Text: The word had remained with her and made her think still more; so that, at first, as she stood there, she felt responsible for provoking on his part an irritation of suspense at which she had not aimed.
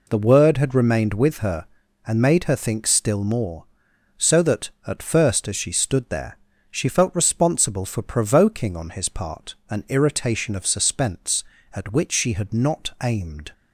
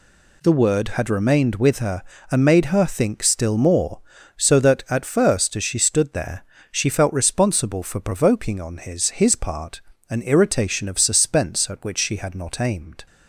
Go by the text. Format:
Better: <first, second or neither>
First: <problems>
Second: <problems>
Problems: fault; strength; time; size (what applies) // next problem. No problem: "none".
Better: first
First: none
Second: says "his" twice; at 9.0 s // pauses between "part" and "an"; slight; at 9.7 s; 0.30 s long